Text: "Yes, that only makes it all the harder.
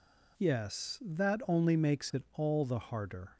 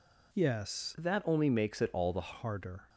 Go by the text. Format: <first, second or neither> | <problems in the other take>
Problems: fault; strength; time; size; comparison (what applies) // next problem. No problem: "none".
first | changes voice from "that" to "the"; from 0.9 to 2.3 s; 1.4 s long